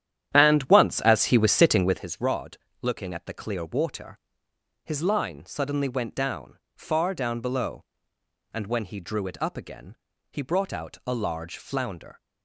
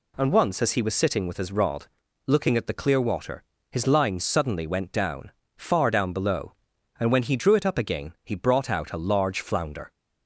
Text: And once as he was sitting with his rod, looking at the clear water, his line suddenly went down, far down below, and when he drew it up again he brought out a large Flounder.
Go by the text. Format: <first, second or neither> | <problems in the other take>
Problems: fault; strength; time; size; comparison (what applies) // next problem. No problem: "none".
second | starts louder than the rest; strong; until 2.1 s; 10.5 dB // pauses between "again" and "he"; slight; at 9.9 s; 0.36 s long